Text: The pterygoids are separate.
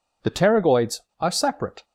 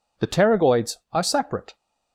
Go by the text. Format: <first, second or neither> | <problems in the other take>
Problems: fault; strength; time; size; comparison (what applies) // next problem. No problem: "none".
neither | none